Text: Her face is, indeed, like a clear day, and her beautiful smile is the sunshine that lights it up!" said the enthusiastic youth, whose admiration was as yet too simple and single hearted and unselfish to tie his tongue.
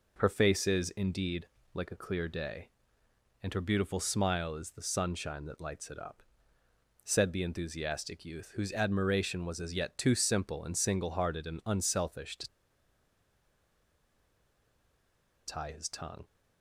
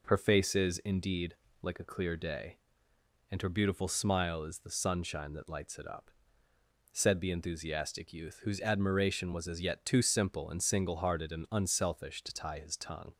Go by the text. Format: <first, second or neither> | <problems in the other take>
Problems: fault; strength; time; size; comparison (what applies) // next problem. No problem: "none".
second | pauses between "to" and "tie"; strong; at 12.4 s; 2.9 s long